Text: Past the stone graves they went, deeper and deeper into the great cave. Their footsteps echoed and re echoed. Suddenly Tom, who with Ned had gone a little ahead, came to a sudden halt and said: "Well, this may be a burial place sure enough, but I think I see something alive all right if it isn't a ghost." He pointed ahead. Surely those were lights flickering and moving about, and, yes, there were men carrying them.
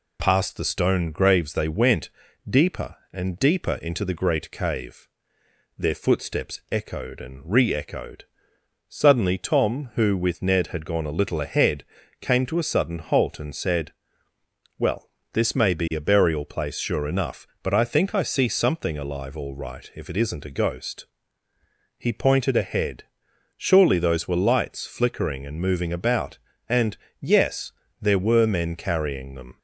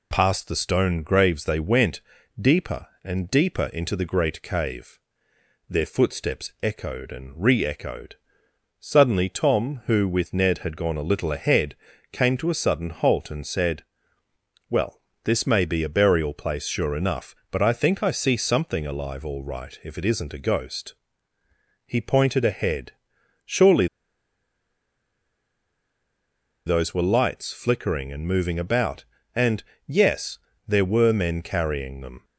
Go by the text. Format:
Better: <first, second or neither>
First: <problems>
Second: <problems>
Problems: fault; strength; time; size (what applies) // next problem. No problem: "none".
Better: first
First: none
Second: pauses between "Surely" and "those"; strong; at 23.8 s; 2.8 s long